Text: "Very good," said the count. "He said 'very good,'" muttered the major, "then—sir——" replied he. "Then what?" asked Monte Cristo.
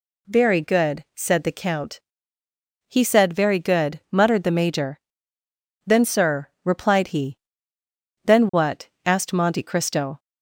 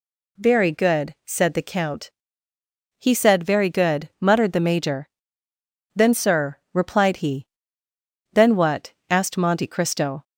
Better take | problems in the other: neither | none

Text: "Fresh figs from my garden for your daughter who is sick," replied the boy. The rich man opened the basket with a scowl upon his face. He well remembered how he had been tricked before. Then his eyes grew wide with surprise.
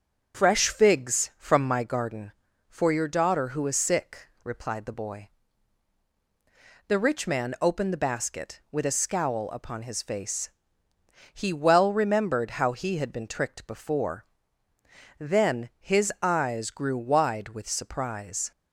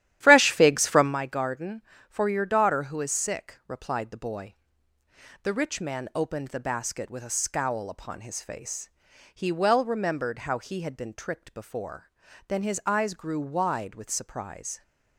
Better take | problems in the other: first | starts louder than the rest; strong; until 1.1 s; 12.5 dB

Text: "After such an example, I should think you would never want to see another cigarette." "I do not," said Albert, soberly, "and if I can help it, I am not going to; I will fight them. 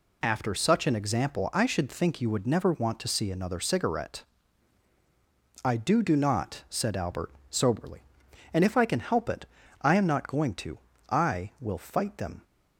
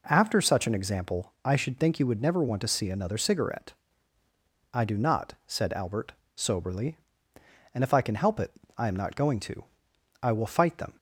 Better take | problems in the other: second | says "do" twice; at 6.0 s

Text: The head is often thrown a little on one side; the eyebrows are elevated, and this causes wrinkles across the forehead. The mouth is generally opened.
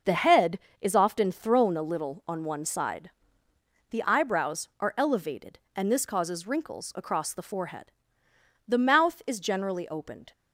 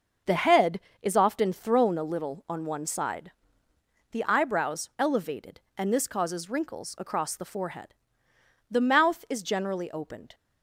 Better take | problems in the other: first | starts louder than the rest; noticeable; until 1.4 s; 6 dB // skips "are"; at 4.9 s

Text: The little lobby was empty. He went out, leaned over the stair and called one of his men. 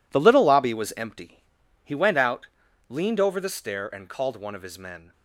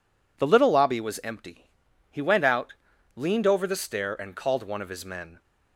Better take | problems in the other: second | gets quieter; strong; throughout; 12.5 dB

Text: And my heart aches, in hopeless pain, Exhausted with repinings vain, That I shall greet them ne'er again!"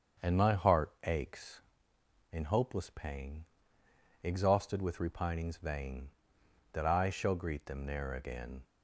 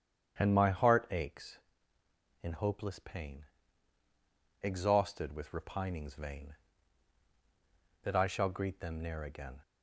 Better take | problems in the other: neither | starts louder than the rest; the same in both

